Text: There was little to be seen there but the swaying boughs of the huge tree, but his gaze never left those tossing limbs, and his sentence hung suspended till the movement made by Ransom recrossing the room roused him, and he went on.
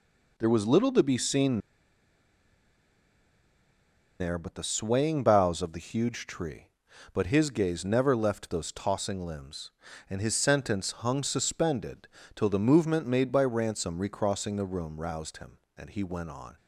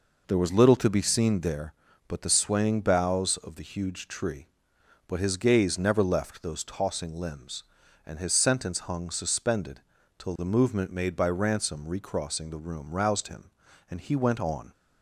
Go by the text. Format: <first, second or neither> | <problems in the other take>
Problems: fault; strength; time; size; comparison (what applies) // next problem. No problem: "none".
second | pauses between "seen" and "there"; strong; at 1.5 s; 2.6 s long // pauses between "suspended" and "till"; slight; at 12.0 s; 0.30 s long; also in the second